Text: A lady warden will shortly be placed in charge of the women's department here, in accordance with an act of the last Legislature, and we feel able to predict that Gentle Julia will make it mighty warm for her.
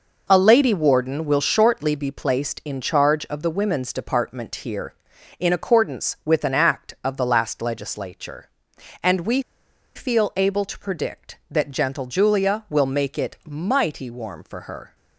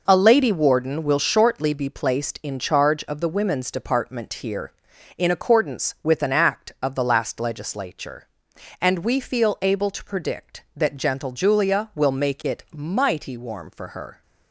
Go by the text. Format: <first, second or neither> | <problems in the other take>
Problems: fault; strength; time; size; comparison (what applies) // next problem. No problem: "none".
second | pauses between "we" and "feel"; noticeable; at 9.4 s; 0.55 s long